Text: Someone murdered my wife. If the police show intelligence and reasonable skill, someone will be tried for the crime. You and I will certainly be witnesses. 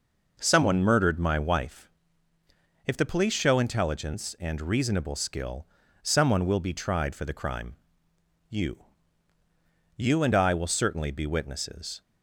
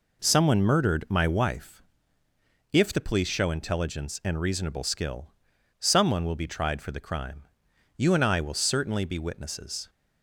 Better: second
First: says "You" twice; at 9.9 s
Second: none

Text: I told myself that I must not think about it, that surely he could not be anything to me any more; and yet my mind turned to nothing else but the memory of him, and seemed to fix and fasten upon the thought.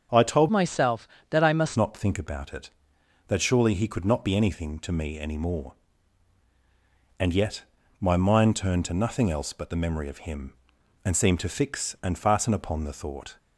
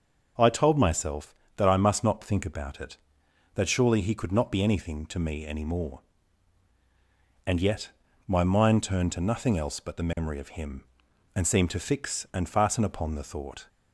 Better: second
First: starts louder than the rest; strong; until 1.3 s; 7 dB // changes voice from "myself" to "must"; from 0.5 to 1.7 s; 1.2 s long // pauses between "yet" and "my"; slight; at 7.6 s; 0.36 s long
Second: starts louder than the rest; until 1.6 s; 6 dB // pauses between "yet" and "my"; slight; at 7.9 s; 0.36 s long

